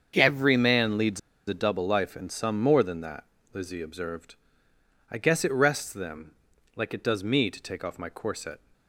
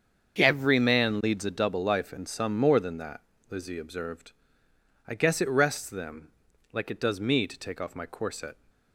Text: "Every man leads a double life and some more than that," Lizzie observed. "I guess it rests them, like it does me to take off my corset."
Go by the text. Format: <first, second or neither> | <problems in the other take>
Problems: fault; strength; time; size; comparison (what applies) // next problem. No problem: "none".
second | starts louder than the rest; until 1.1 s; 7 dB; also in the second // pauses between "leads" and "a"; slight; at 1.1 s; 0.27 s long